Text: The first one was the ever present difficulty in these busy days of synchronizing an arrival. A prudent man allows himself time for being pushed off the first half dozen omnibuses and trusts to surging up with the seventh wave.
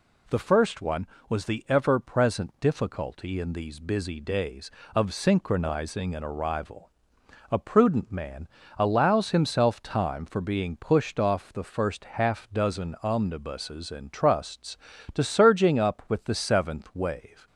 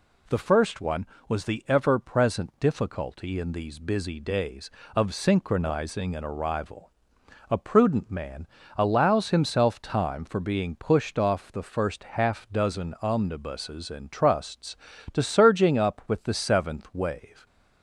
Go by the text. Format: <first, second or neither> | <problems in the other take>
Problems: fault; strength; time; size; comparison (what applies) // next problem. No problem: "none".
neither | pauses between "man" and "allows"; slight; the same in both